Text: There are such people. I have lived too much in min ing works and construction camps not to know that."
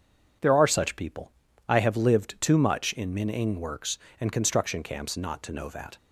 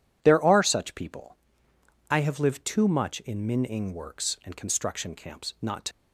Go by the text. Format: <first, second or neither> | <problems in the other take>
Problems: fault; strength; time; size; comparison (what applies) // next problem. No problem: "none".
first | stops before "know that"; at 5.9 s